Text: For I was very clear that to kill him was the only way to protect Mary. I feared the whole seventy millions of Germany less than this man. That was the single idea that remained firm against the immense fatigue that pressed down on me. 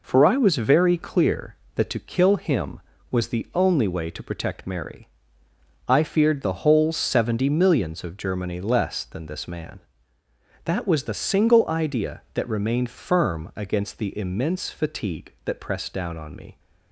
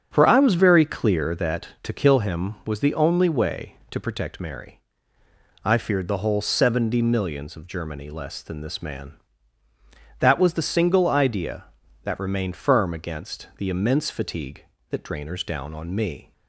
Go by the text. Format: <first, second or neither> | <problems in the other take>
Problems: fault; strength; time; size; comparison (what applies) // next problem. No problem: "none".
first | starts louder than the rest; strong; until 1.1 s; 8 dB // says "drainers" for "pressed"; at 15.0 s